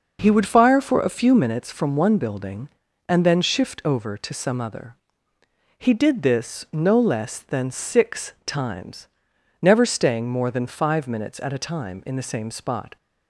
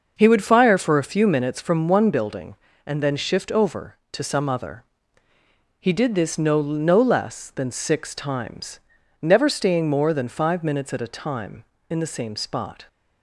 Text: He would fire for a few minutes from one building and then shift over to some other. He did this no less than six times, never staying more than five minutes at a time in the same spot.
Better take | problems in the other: first | starts louder than the rest; noticeable; until 1.1 s; 6 dB // says "no" twice; at 6.5 s

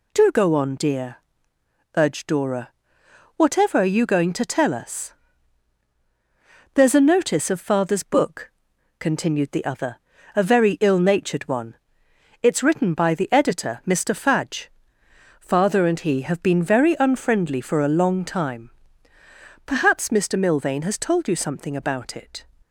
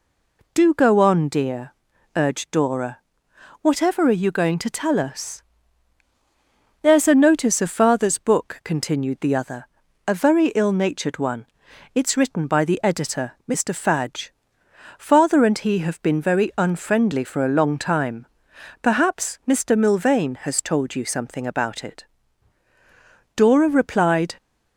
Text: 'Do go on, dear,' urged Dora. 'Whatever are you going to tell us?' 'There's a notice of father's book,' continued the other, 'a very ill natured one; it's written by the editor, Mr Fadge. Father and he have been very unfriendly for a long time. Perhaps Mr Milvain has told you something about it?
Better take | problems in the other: first | stays silent before the first word; slight; until 0.5 s; 0.5 s long // goes on to say "Dora replied"; noticeable; from 23.3 s on; 1.0 s long

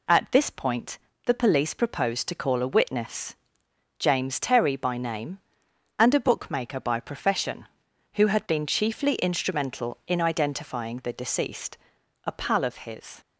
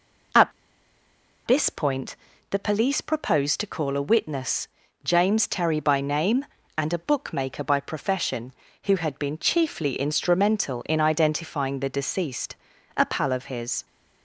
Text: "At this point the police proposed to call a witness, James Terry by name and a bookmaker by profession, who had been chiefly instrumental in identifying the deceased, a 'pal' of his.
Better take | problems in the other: first | pauses between "At" and "this"; noticeable; at 0.5 s; 0.95 s long // pauses between "point" and "the"; slight; at 2.1 s; 0.32 s long; slight in the first

